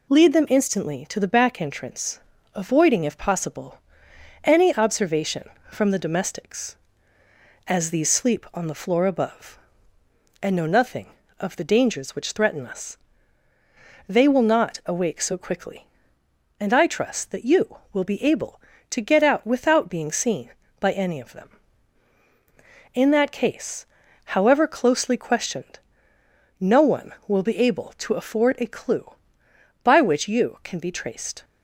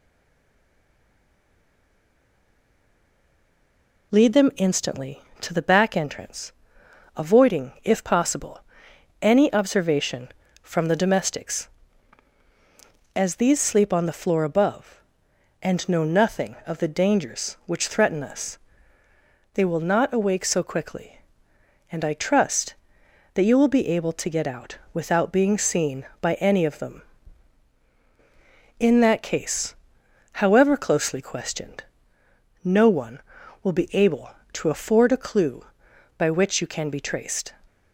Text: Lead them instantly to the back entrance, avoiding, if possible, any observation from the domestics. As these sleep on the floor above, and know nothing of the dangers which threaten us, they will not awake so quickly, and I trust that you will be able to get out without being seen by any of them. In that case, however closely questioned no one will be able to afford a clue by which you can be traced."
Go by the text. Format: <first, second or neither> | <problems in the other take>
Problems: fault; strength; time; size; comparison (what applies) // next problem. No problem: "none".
first | stays silent before the first word; strong; until 4.1 s; 4.1 s long // pauses between "questioned" and "no"; noticeable; at 31.8 s; 0.80 s long; noticeable in the first